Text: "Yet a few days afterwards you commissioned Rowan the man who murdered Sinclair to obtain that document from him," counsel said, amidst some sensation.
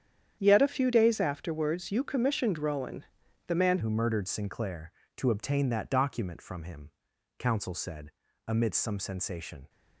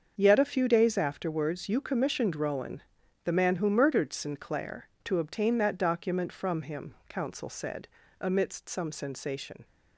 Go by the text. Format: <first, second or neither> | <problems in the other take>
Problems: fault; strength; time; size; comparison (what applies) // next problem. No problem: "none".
second | starts louder than the rest; strong; until 1.4 s; 9 dB; also in the second // pauses between "Rowan" and "the"; noticeable; at 3.0 s; 0.46 s long; noticeable in the second // changes voice at "who"; from 3.8 s on; 5.8 s long